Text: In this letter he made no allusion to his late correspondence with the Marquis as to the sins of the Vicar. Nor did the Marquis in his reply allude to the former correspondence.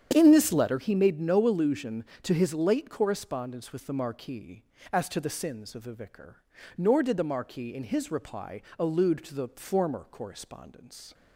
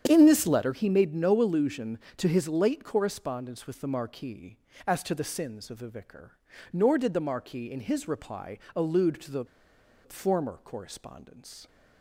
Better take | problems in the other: first | starts louder than the rest; strong; until 1.0 s; 8.5 dB; strong in the first // pauses between "reply" and "allude"; slight; at 8.5 s; 0.18 s long; slight in the first // pauses between "the" and "former"; noticeable; at 9.4 s; 0.57 s long

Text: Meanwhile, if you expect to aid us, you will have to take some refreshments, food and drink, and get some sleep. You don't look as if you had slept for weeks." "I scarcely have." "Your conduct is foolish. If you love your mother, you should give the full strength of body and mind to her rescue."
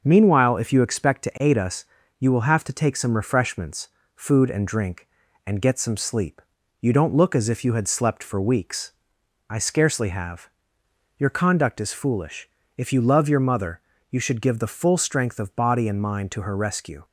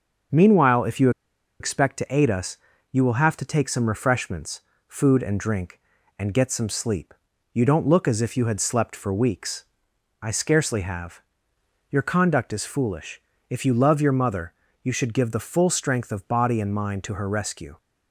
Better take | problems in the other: first | starts louder than the rest; until 1.8 s; 6.5 dB; noticeable in the first // pauses between "you" and "expect"; noticeable; at 1.0 s; 0.50 s long

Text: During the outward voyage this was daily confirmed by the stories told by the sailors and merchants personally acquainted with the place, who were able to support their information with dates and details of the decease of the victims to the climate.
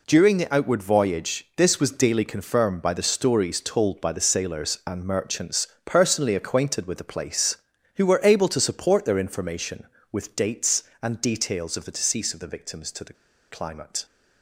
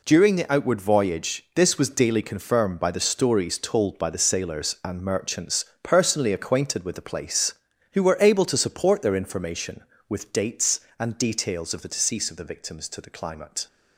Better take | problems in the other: second | pauses between "merchants" and "personally"; slight; at 5.6 s; 0.20 s long; slight in the second // pauses between "the" and "climate"; at 13.1 s; 0.36 s long

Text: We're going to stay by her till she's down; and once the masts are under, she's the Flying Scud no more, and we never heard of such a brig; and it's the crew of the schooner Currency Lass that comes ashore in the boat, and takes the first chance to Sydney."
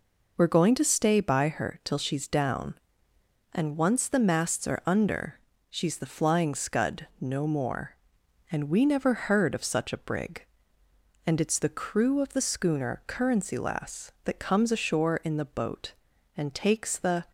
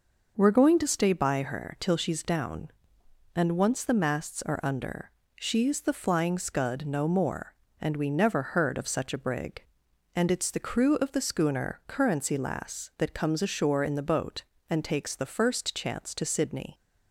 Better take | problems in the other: second | stops before "first chance to Sydney"; at 17.2 s

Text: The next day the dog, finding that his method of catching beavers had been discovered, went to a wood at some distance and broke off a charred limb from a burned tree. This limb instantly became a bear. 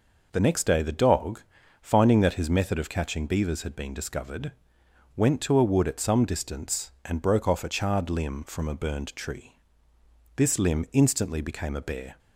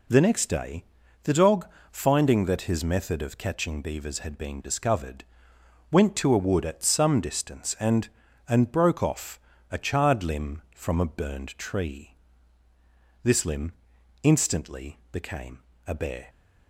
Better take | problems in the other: first | pauses between "day" and "the"; at 0.8 s; 0.40 s long // says "and" twice; at 8.4 s // pauses between "off" and "a"; slight; at 9.3 s; 0.32 s long // pauses between "limb" and "instantly"; noticeable; at 13.7 s; 0.50 s long // pauses between "became" and "a"; slight; at 15.5 s; 0.28 s long

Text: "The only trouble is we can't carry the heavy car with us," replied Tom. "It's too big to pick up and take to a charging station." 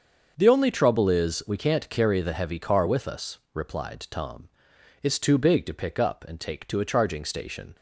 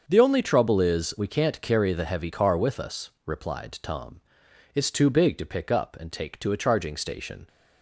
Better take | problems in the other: neither | starts louder than the rest; the same in both

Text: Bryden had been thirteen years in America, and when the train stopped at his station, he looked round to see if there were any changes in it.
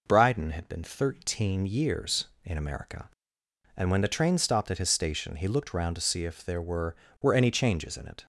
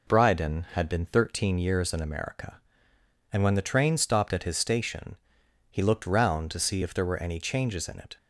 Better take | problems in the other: second | says "were" twice; at 7.2 s

